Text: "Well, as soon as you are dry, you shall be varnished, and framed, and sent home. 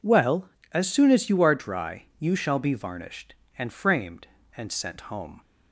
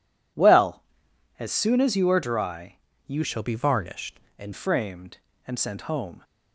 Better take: first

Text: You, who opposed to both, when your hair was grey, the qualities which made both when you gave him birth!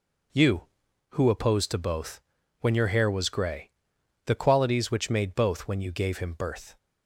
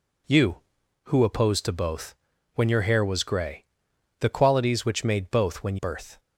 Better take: first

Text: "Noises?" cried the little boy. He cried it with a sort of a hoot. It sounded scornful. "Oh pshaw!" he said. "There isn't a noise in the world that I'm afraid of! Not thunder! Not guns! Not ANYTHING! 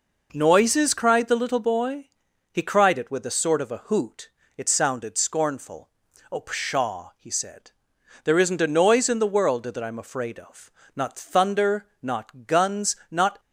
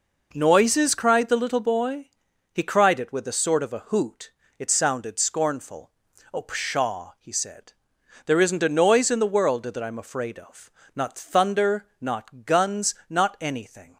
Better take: second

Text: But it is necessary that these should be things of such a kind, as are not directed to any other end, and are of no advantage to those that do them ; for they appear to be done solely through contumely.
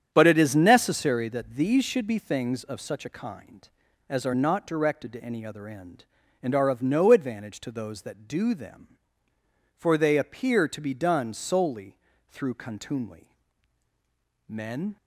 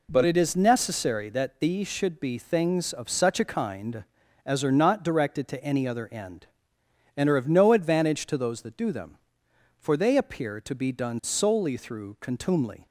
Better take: second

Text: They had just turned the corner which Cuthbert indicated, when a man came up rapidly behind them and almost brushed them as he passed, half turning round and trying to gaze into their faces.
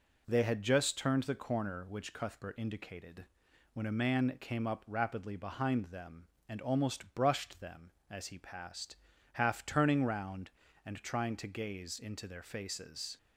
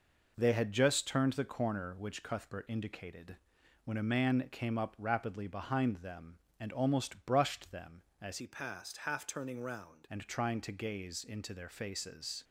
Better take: first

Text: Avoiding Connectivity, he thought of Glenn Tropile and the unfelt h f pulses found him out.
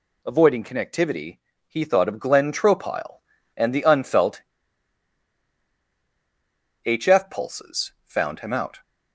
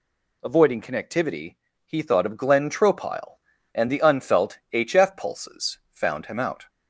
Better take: second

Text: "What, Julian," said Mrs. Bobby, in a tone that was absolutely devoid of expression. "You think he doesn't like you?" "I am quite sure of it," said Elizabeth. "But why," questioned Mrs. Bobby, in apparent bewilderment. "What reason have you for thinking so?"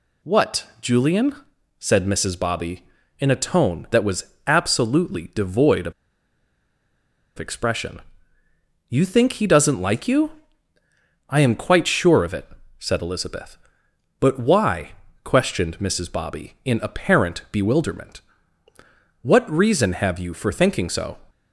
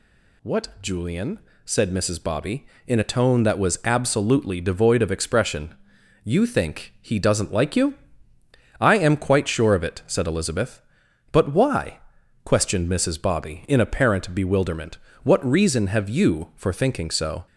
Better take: second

